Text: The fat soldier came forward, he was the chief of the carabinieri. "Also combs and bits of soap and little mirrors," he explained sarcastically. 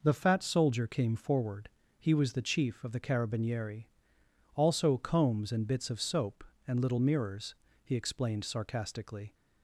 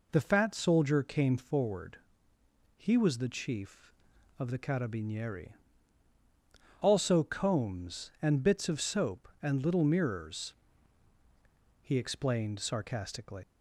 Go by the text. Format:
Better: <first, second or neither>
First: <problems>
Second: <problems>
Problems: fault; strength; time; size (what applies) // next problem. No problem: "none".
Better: first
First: none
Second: leaves "sarcastically" unfinished; at 13.4 s; 130 ms